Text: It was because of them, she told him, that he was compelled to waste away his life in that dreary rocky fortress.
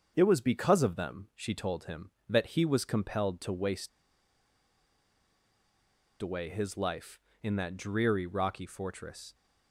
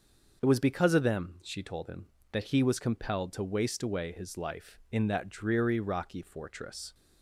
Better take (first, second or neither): second